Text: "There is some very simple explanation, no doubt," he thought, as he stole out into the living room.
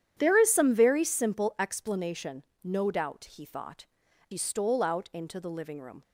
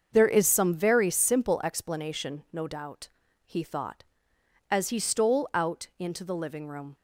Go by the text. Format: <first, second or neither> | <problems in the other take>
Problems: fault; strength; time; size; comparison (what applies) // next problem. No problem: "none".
second | starts louder than the rest; strong; until 1.1 s; 9.5 dB; also in the second // skips "as"; at 4.0 s